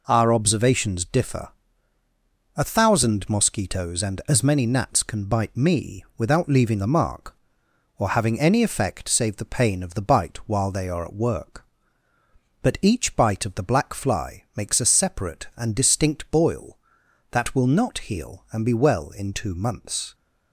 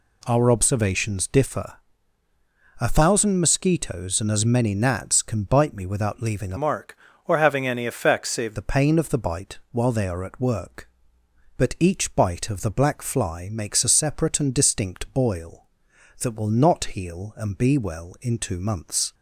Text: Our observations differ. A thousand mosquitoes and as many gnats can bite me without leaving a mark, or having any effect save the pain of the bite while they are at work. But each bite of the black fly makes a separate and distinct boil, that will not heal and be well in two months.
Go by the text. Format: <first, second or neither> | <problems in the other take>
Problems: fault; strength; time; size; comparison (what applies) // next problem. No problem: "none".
first | changes voice from "mark" to "save"; from 6.5 to 8.5 s; 2.0 s long